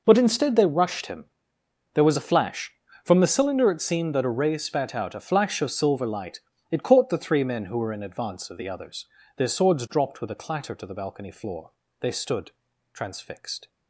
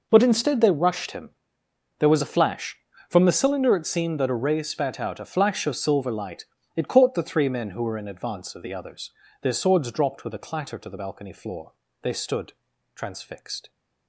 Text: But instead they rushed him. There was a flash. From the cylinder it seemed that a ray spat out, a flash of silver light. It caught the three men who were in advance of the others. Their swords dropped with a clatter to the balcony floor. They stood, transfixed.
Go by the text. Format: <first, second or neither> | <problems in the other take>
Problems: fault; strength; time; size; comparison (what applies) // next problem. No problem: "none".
neither | none